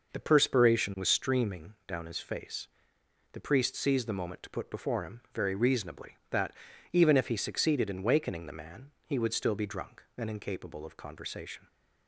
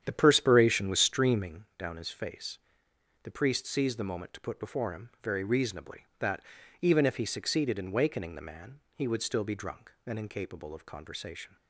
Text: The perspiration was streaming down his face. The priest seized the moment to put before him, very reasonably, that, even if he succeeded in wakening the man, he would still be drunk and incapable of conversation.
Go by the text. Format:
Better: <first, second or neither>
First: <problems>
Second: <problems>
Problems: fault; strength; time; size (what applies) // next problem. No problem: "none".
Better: first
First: none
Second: starts louder than the rest; strong; until 1.6 s; 9 dB